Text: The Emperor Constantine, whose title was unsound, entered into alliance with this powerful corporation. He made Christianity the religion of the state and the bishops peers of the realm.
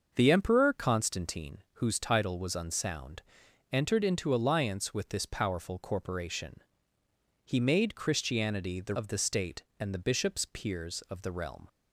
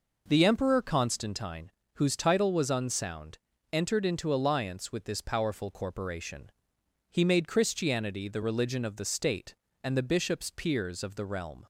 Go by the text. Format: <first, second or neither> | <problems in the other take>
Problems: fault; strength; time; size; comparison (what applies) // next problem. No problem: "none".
second | starts louder than the rest; until 1.1 s; 6.5 dB // skips "religion"; at 8.9 s